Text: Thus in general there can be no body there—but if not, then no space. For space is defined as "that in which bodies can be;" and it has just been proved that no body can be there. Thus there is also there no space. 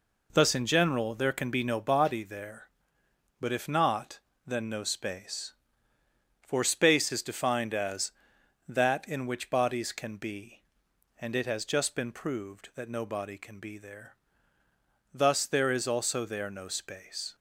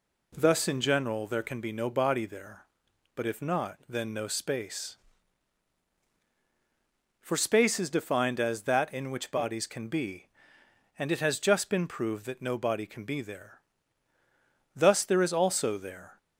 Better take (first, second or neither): first